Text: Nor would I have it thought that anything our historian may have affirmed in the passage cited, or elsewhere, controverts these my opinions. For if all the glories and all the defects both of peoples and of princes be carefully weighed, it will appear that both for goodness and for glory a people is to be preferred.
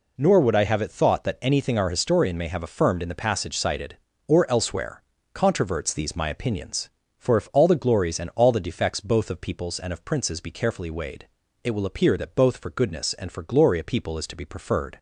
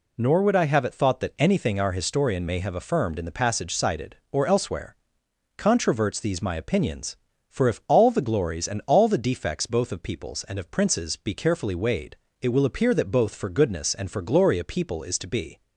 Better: first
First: none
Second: stops before "preferred"; at 15.6 s

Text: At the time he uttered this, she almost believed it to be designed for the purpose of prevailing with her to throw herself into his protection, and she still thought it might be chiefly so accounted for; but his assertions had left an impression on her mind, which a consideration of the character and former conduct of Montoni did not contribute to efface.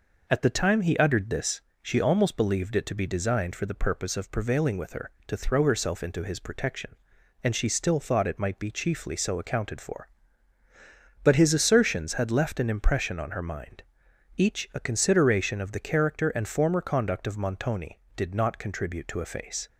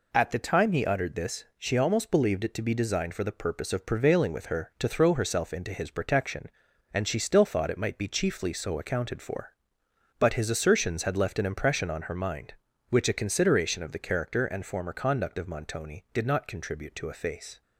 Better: second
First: says "each" for "which"; at 14.3 s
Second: none

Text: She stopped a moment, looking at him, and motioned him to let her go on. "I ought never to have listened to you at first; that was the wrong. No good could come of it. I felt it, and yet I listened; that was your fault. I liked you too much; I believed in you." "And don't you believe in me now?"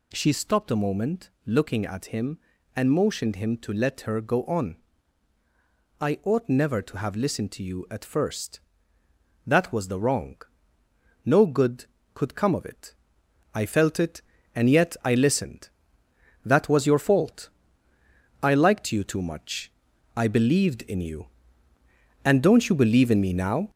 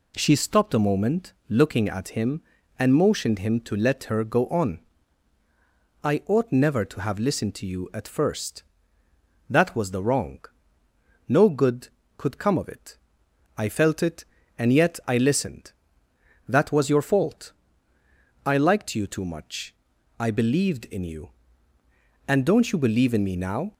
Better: second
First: gets louder; throughout; 3.5 dB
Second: none

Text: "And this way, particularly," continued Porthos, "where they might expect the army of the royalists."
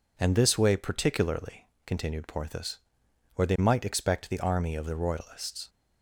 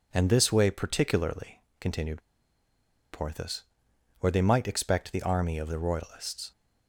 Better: first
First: none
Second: pauses between "continued" and "Porthos"; noticeable; at 2.2 s; 0.91 s long

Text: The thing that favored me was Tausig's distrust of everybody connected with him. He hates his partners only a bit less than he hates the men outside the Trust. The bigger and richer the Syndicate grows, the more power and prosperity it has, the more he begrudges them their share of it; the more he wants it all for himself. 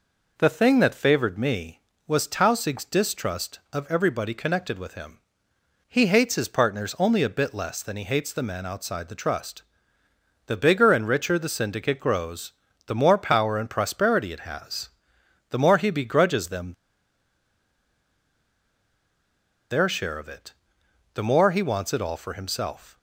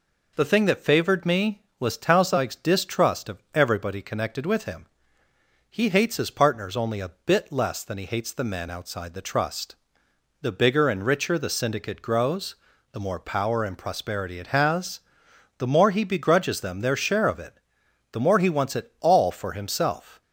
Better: second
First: pauses between "them" and "their"; strong; at 16.7 s; 2.9 s long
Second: none

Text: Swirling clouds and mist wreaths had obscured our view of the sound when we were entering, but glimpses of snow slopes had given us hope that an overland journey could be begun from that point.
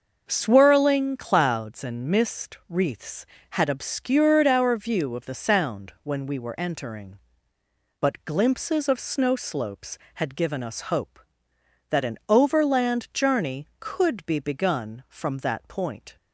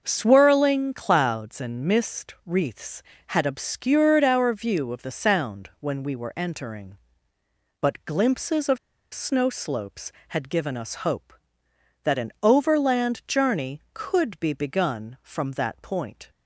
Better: first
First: starts louder than the rest; noticeable; until 1.2 s; 6 dB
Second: starts louder than the rest; noticeable; until 1.0 s; 6 dB // pauses between "of" and "snow"; at 8.7 s; 0.36 s long

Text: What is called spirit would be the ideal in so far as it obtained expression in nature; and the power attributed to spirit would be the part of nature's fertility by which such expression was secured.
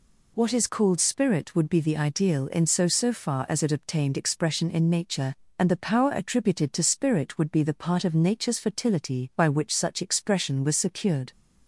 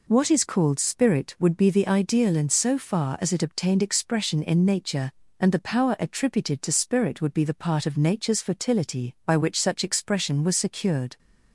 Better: second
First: says "so" twice; at 2.8 s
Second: none

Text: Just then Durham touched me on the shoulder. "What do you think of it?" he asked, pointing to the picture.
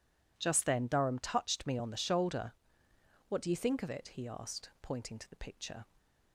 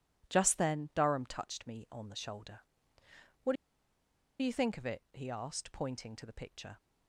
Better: first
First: none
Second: pauses between "do" and "you"; noticeable; at 3.5 s; 0.87 s long

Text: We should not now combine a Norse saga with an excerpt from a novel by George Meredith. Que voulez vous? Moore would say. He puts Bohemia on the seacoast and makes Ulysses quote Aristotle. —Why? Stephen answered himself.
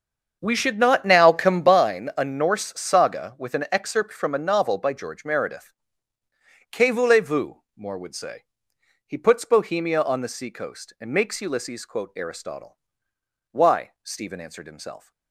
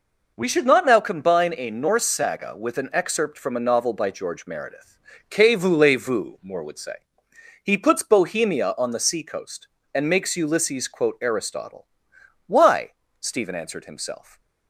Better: second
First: starts louder than the rest; until 1.8 s; 7 dB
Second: none

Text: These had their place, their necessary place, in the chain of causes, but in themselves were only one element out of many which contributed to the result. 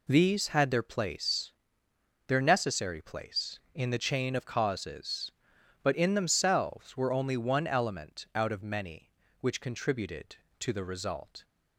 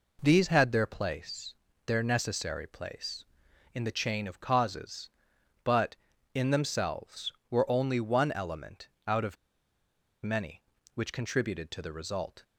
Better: first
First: none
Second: pauses between "element" and "out"; slight; at 8.8 s; 0.20 s long // pauses between "of" and "many"; noticeable; at 9.3 s; 0.89 s long

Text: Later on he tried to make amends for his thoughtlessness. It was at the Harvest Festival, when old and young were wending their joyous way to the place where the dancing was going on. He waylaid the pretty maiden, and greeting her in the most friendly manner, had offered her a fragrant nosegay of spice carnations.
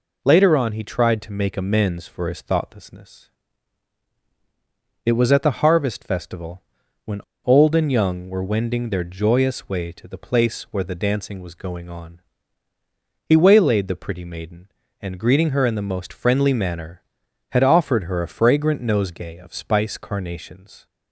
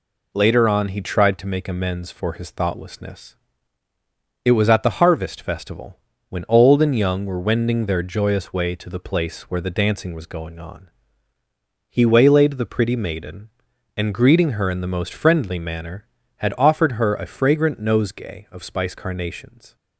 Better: second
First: pauses between "when" and "old"; slight; at 7.2 s; 0.23 s long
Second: none

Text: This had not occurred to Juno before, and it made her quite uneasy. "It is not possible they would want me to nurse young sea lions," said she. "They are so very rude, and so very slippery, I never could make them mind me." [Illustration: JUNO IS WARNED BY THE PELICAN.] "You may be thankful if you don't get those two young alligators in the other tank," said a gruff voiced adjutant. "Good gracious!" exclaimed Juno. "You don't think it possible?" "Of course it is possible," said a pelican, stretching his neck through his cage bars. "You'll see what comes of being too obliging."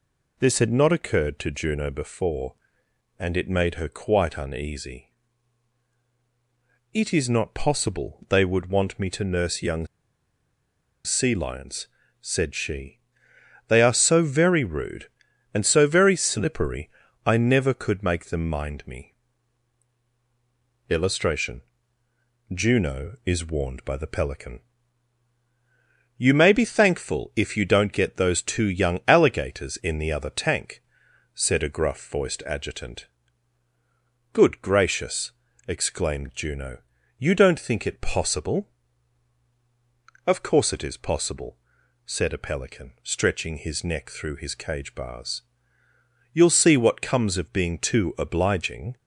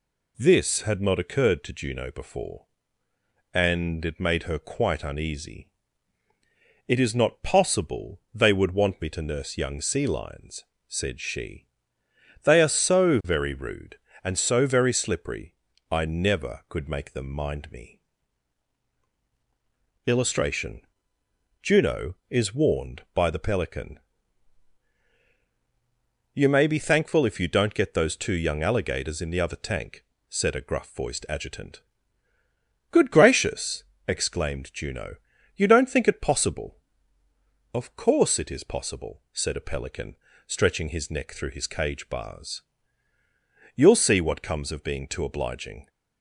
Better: second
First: pauses between "young" and "sea"; at 9.8 s; 1.1 s long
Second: none

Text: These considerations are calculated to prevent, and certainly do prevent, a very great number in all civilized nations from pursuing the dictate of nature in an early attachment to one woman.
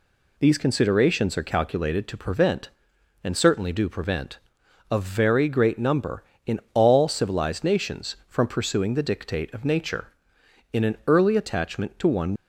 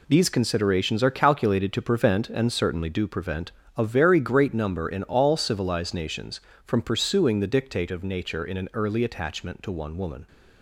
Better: second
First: stops before "woman"; at 12.3 s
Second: none

